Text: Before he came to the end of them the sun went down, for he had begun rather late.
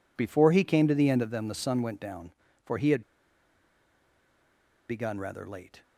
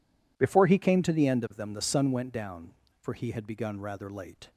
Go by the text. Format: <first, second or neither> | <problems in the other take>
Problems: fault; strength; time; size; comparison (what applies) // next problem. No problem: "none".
second | pauses between "had" and "begun"; strong; at 3.0 s; 1.8 s long